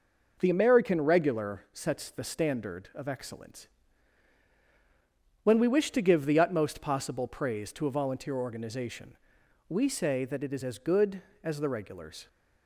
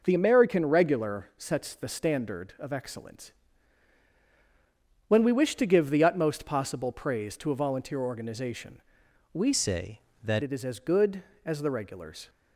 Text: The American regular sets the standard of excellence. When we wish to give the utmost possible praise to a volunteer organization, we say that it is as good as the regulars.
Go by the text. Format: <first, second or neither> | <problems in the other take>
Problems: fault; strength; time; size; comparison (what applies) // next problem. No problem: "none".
first | changes voice from "say" to "that"; from 9.5 to 10.4 s; 0.9 s long